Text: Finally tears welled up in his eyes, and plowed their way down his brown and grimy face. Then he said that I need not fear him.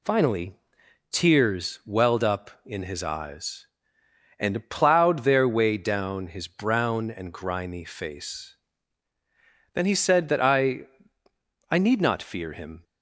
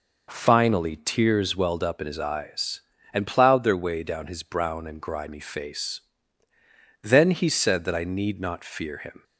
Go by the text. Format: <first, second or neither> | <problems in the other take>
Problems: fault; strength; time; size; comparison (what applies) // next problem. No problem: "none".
second | pauses between "Finally" and "tears"; noticeable; at 0.5 s; 0.58 s long // says "I" twice; at 11.6 s